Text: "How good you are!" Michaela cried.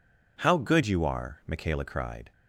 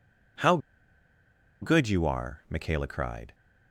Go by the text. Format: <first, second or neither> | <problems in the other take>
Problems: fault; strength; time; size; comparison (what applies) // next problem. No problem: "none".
first | pauses between "How" and "good"; at 0.5 s; 1.0 s long